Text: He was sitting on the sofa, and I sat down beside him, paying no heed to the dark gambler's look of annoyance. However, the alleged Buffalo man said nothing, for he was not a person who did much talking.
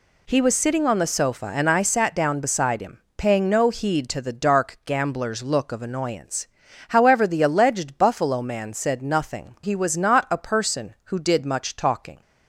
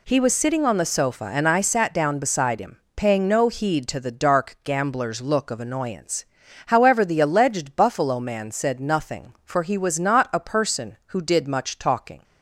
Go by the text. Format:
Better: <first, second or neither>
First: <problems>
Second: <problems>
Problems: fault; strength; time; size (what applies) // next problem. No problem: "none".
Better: second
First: skips "for"; at 9.5 s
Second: none